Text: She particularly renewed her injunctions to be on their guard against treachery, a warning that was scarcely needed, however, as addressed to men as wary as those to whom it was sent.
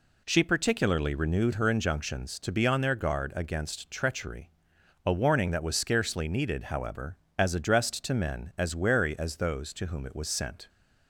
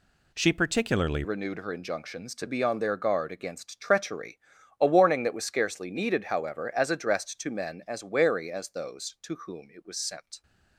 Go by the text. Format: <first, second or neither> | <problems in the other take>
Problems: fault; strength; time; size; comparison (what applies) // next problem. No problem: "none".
first | changes voice at "renewed"; from 1.2 s on; 9.2 s long